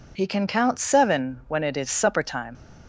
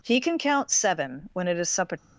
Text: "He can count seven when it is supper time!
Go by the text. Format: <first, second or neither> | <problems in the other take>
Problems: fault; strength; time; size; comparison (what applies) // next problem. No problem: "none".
first | stops before "time"; at 1.9 s